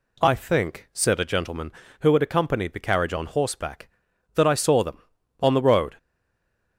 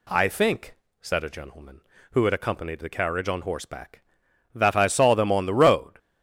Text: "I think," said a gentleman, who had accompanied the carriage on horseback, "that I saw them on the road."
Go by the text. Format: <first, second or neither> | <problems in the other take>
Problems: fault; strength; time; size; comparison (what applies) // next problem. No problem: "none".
second | stays silent after the last word; slight; from 5.9 s on; 0.8 s long